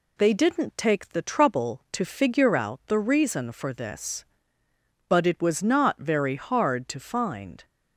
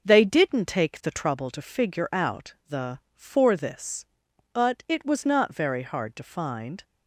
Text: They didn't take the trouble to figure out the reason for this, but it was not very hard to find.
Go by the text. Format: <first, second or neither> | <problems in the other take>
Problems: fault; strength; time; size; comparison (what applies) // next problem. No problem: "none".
first | pauses between "out" and "the"; slight; at 2.5 s; 0.16 s long // skips "reason"; at 3.0 s